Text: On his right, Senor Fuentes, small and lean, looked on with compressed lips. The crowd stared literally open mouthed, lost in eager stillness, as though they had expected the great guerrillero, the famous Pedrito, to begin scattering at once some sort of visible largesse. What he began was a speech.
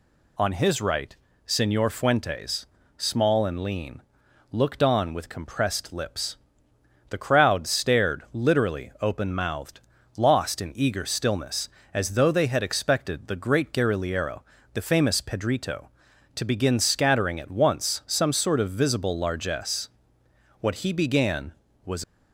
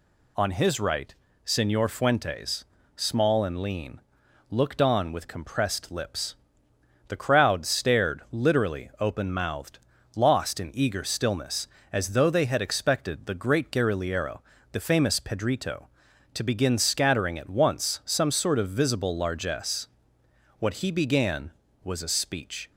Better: second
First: stops before "a speech"; at 22.0 s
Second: none

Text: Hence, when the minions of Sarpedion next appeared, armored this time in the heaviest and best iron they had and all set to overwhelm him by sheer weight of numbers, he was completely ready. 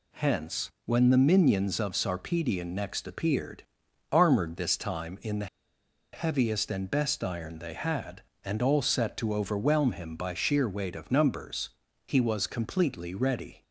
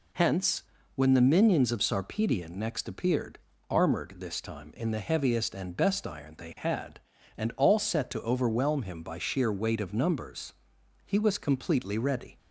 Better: second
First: pauses between "the" and "heaviest"; noticeable; at 5.4 s; 0.67 s long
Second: none

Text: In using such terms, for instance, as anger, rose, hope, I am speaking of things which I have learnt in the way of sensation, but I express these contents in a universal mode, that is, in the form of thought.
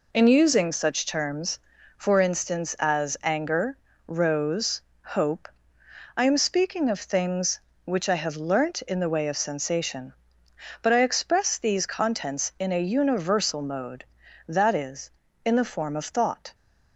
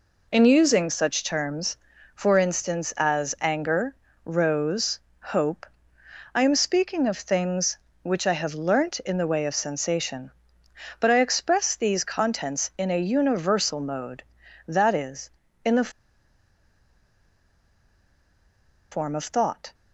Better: first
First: none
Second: pauses between "the" and "form"; strong; at 15.9 s; 3.0 s long

